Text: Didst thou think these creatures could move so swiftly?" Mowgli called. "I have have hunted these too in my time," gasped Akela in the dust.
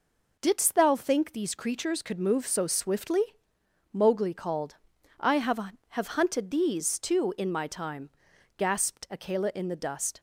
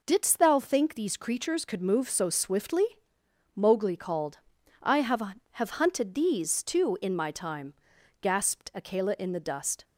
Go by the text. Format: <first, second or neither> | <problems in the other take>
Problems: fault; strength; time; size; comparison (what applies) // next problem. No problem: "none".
neither | none